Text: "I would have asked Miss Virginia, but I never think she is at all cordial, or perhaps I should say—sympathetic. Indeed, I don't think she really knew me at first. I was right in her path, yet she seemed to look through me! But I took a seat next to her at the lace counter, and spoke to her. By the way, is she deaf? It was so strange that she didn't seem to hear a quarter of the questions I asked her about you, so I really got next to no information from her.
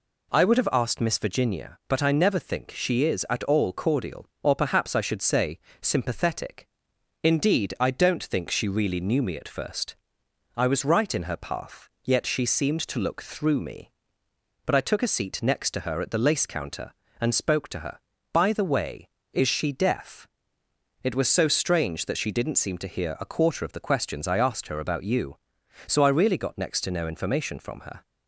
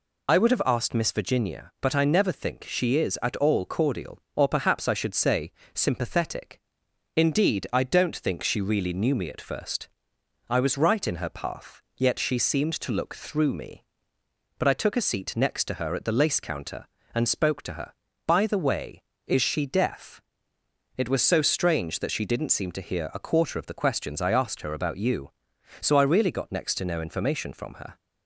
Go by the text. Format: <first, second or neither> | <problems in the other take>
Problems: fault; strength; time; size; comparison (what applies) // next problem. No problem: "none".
first | loses the start of "I"; at 0.2 s; 45 ms